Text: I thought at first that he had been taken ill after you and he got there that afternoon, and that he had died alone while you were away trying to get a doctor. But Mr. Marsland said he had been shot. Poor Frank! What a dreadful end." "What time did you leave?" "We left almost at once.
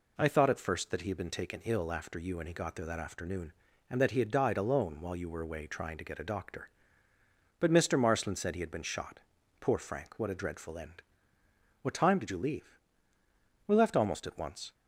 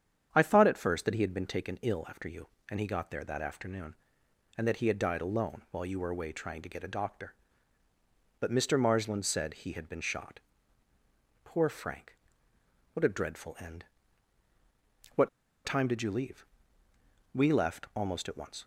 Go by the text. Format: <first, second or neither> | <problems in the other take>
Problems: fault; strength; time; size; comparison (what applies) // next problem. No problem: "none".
first | starts louder than the rest; strong; until 1.3 s; 8.5 dB // pauses between "What" and "time"; at 15.2 s; 0.36 s long